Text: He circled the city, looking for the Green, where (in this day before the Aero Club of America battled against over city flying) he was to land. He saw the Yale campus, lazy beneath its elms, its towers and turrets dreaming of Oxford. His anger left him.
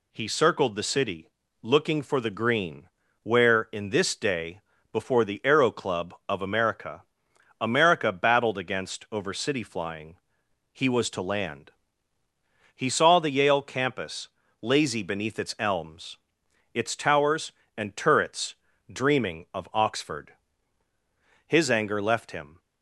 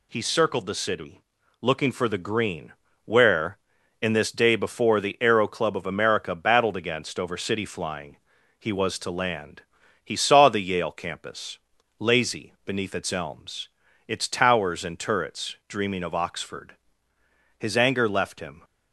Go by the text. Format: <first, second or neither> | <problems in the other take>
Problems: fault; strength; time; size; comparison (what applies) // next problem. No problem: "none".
second | pauses between "day" and "before"; slight; at 4.5 s; 0.32 s long // says "America" twice; at 7.6 s // pauses between "turrets" and "dreaming"; slight; at 18.5 s; 0.36 s long